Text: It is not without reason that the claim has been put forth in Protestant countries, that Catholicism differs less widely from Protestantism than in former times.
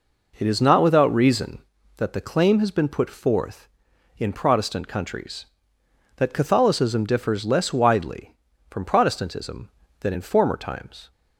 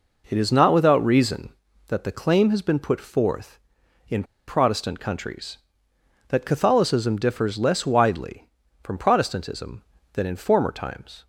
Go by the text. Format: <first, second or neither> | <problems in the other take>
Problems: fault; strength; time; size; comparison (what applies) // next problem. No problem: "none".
first | pauses between "in" and "Protestant"; slight; at 4.2 s; 0.24 s long